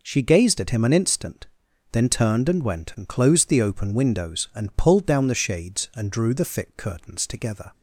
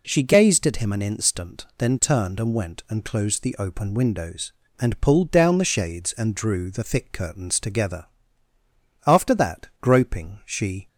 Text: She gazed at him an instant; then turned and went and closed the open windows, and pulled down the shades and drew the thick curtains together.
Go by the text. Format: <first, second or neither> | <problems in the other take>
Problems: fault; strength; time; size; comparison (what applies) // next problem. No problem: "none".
first | goes on to say "After that groping she"; strong; from 9.0 s on; 1.8 s long